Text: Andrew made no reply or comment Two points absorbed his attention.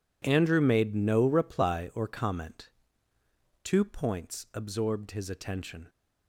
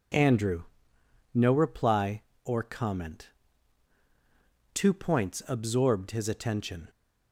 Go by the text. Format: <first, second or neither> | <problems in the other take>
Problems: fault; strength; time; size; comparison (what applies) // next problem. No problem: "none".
first | skips "made"; at 0.9 s // pauses between "comment" and "Two"; strong; at 3.2 s; 1.4 s long; noticeable in the first